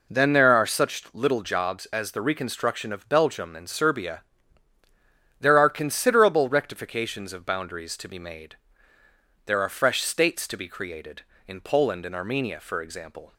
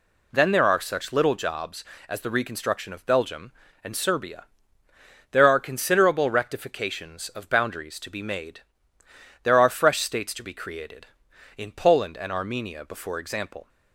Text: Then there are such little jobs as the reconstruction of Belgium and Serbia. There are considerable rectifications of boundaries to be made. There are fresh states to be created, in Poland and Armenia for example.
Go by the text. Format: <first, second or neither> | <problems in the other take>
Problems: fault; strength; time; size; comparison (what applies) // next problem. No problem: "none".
first | says "before" for "for"; at 12.8 s